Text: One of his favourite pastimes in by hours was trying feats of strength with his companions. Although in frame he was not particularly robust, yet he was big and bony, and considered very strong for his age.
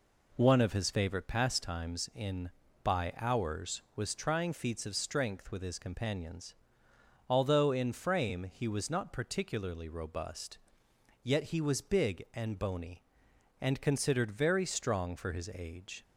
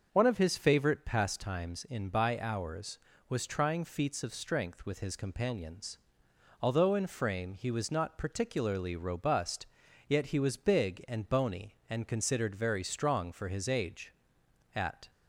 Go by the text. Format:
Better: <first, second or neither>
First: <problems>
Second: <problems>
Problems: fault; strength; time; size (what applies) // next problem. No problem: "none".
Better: first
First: none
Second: starts louder than the rest; until 1.1 s; 6.5 dB // goes on to say "At"; slight; from 14.7 s on; 0.36 s long